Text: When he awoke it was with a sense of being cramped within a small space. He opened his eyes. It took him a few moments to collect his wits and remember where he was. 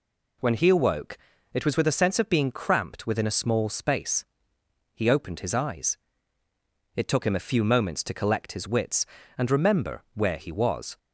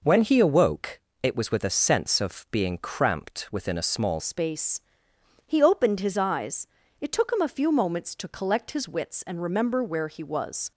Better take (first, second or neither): first